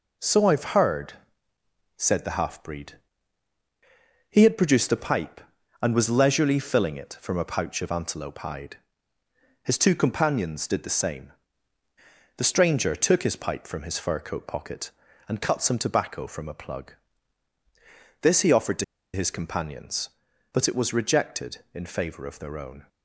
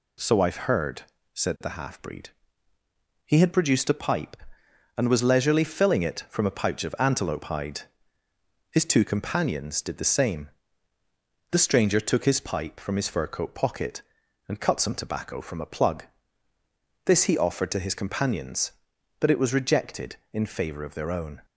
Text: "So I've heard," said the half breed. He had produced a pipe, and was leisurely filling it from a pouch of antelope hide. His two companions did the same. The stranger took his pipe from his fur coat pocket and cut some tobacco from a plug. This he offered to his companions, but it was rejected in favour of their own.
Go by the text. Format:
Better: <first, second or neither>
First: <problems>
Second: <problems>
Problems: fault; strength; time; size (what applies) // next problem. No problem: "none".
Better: second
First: pauses between "to" and "his"; slight; at 18.8 s; 0.29 s long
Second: none